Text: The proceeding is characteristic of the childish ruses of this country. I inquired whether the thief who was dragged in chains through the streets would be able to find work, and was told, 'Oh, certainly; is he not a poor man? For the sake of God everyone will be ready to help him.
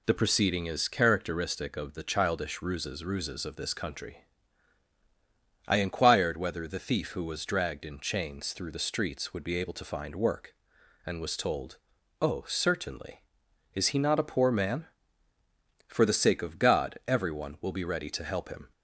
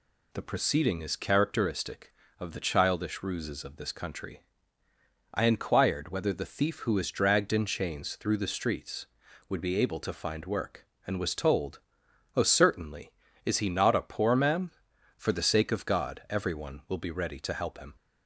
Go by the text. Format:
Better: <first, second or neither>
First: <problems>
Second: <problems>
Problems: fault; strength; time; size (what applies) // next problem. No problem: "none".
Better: second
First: says "ruses" twice; at 3.0 s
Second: none